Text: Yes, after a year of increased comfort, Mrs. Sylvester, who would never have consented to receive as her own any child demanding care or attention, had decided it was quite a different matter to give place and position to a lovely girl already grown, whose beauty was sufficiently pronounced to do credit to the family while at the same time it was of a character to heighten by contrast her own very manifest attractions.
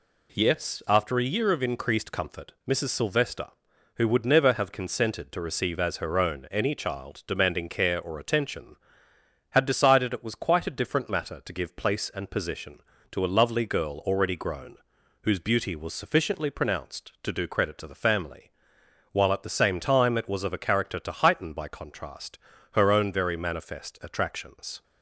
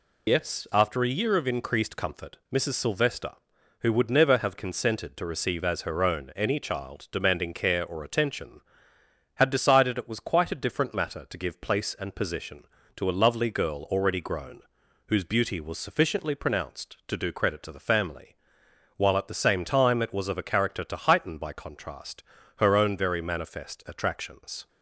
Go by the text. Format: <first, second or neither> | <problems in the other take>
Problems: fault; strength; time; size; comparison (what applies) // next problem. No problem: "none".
first | loses the start of "Yes"; at 0.2 s; 110 ms // pauses between "family" and "while"; noticeable; at 18.3 s; 0.66 s long; noticeable in the first // pauses between "contrast" and "her"; slight; at 22.2 s; 0.36 s long; slight in the first